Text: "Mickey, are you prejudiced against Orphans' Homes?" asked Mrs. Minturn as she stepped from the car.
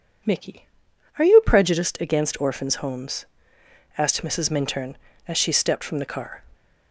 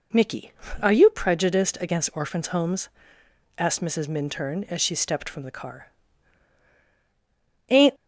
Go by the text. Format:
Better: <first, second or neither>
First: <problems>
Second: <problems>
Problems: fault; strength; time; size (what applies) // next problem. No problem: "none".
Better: first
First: none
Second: goes on to say "Ain't"; slight; from 7.6 s on; 0.26 s long